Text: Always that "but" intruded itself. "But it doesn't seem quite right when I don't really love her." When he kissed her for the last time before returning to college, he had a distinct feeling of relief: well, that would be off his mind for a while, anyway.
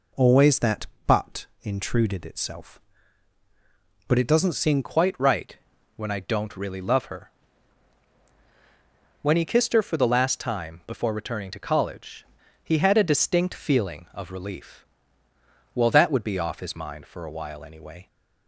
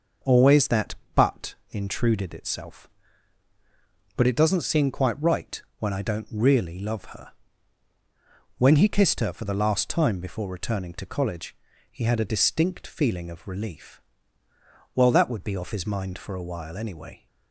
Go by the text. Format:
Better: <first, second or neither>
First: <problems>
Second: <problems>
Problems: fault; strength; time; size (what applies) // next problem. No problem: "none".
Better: second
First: changes voice at "quite"; from 4.8 s on; 13.2 s long // pauses between "right" and "when"; at 5.5 s; 0.40 s long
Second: pauses between "right" and "when"; slight; at 5.6 s; 0.20 s long